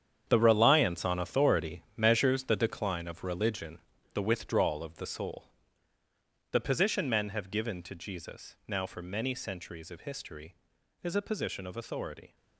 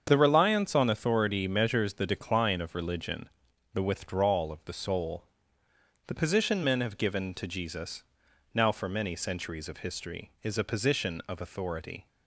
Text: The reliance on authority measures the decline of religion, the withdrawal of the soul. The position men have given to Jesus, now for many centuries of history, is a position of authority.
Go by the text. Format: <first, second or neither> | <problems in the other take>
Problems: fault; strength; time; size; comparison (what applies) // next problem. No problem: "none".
second | gets quieter; strong; throughout; 11.5 dB // starts louder than the rest; strong; until 1.2 s; 8.5 dB; strong in the second